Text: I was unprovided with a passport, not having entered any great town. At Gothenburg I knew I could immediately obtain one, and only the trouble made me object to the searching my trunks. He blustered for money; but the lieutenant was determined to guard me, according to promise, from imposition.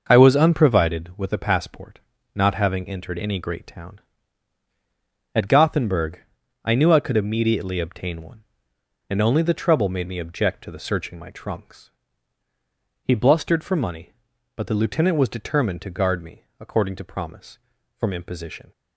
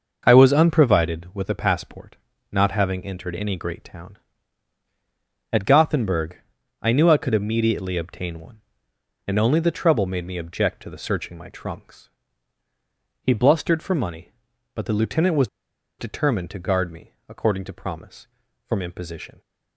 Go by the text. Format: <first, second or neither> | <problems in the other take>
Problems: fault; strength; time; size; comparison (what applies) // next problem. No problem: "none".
first | starts louder than the rest; noticeable; until 1.2 s; 6 dB // pauses between "Gothenburg" and "I"; at 6.3 s; 0.42 s long; also in the first // pauses between "was" and "determined"; noticeable; at 15.4 s; 0.52 s long